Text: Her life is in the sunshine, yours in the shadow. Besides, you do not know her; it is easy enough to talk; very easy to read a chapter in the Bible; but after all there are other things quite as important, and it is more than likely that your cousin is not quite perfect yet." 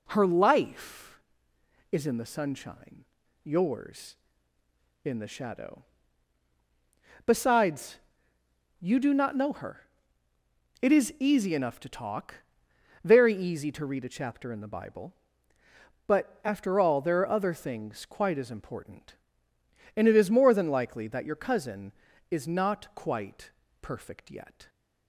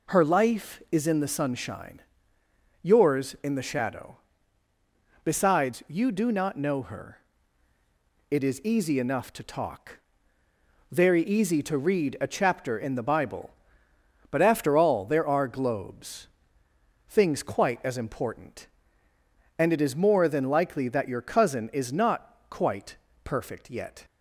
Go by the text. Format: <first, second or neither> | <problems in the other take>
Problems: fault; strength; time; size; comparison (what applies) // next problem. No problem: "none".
first | says "globes" for "other"; at 15.4 s // pauses between "quite" and "perfect"; slight; at 22.9 s; 0.26 s long; slight in the first